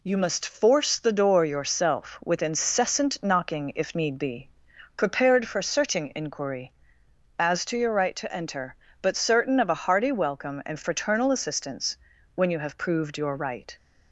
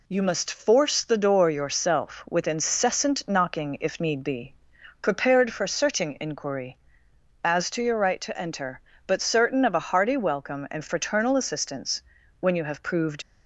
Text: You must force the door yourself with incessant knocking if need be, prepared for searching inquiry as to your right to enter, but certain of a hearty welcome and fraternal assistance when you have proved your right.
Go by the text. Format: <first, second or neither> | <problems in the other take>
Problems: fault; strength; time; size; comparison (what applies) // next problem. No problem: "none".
first | pauses between "assistance" and "when"; slight; at 12.0 s; 0.36 s long; slight in the first // stops before "your right"; at 13.2 s